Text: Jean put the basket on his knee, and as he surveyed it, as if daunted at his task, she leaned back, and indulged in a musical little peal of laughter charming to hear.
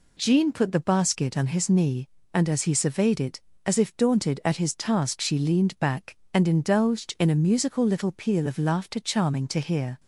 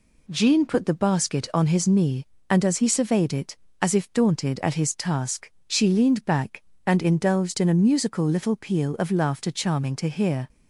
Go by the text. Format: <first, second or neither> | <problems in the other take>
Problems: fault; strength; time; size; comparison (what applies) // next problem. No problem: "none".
neither | none